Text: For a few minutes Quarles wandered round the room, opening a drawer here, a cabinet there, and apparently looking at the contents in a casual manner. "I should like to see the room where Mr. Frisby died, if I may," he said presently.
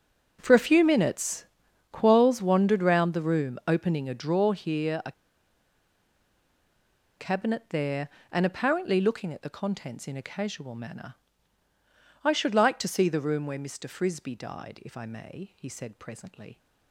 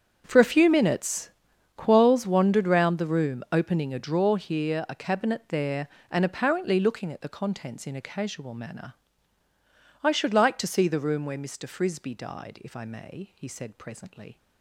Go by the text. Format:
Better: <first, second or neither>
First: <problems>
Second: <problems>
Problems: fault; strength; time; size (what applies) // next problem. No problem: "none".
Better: second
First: starts louder than the rest; strong; until 1.4 s; 7.5 dB // pauses between "minutes" and "Quarles"; noticeable; at 1.4 s; 0.46 s long // pauses between "a" and "cabinet"; strong; at 5.1 s; 2.0 s long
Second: starts louder than the rest; strong; until 1.2 s; 7 dB // pauses between "minutes" and "Quarles"; noticeable; at 1.3 s; 0.46 s long